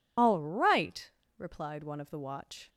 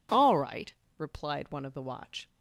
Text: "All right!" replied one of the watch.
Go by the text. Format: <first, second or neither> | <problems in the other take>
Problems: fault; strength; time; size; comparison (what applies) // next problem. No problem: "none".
second | loses the start of "All"; at 0.1 s; 50 ms